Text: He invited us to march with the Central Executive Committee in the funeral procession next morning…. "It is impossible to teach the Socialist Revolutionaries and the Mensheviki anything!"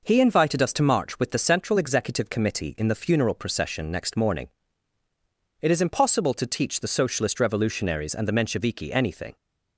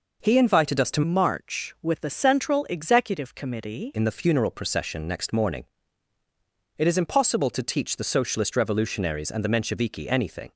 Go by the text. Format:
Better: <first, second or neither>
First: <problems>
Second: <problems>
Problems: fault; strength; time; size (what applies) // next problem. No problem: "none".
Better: first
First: none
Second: changes voice from "march" to "Committee"; from 1.0 to 3.9 s; 2.9 s long